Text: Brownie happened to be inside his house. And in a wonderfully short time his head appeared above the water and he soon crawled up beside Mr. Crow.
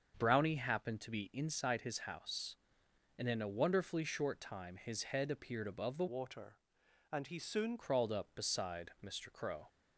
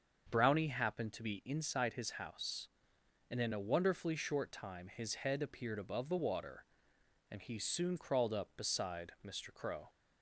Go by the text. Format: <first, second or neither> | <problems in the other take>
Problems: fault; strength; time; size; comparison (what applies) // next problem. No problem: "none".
second | starts louder than the rest; until 1.1 s; 7 dB; also in the second // changes voice from "water" to "soon"; from 6.0 to 7.7 s; 1.7 s long